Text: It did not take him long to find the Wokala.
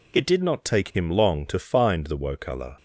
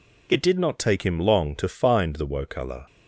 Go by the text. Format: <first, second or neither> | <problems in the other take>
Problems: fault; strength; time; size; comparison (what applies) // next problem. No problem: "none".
neither | none